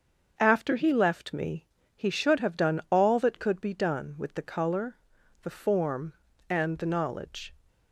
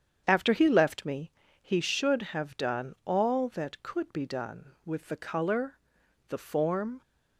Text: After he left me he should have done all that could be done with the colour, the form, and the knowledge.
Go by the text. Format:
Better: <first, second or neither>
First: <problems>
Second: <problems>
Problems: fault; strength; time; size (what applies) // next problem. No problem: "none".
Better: first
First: starts louder than the rest; until 1.3 s; 6.5 dB // pauses between "me" and "he"; slight; at 1.6 s; 0.30 s long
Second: starts louder than the rest; strong; until 1.2 s; 8.5 dB // pauses between "me" and "he"; slight; at 1.3 s; 0.30 s long // stops before "and the knowledge"; at 7.0 s